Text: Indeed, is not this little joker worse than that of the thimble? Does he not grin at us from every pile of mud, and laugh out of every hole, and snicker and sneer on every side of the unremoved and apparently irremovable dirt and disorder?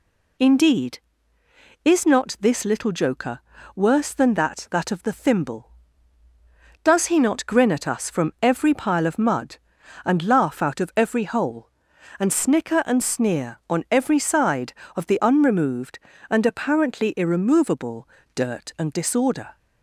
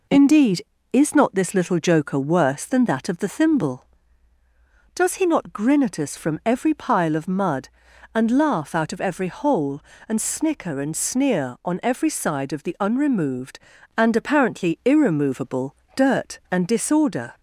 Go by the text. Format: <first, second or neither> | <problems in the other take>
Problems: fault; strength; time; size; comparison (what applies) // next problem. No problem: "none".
second | pauses between "joker" and "worse"; slight; at 3.3 s; 0.36 s long // says "that" twice; at 4.7 s // pauses between "irremovable" and "dirt"; slight; at 18.0 s; 0.28 s long; slight in the second